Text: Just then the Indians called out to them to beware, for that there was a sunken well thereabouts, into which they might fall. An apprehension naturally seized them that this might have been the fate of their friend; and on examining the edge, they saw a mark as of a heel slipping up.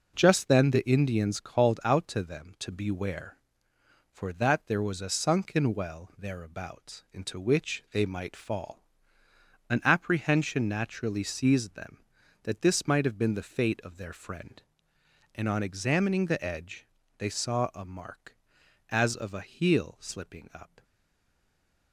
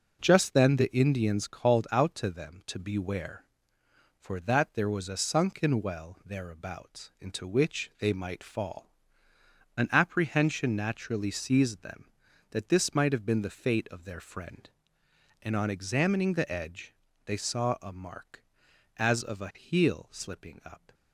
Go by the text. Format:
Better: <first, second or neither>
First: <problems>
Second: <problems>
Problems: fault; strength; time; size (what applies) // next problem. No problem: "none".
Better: second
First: stays silent after the last word; from 20.8 s on; 1.1 s long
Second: none